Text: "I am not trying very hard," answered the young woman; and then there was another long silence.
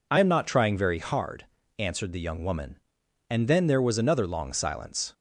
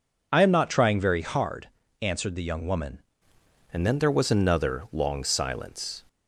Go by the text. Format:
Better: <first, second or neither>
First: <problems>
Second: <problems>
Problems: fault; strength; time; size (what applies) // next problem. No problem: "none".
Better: first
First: none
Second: changes voice at "and"; from 3.7 s on; 2.3 s long